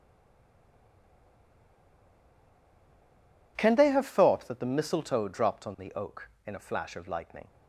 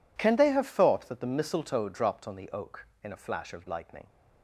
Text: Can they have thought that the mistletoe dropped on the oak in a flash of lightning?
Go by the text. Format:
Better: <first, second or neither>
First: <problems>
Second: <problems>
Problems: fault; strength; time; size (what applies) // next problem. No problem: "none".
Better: second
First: stays silent before the first word; strong; until 3.5 s; 3.5 s long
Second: none